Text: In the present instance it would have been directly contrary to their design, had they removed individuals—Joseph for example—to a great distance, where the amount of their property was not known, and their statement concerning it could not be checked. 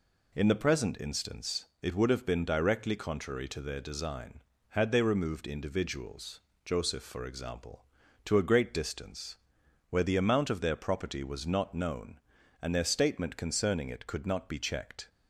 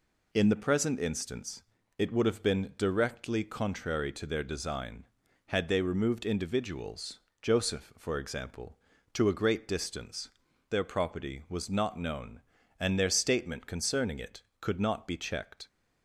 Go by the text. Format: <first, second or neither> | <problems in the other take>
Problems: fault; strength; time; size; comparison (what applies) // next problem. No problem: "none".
first | pauses between "instance" and "it"; slight; at 1.6 s; 0.36 s long; slight in the first // skips "where the amount of"; at 10.5 s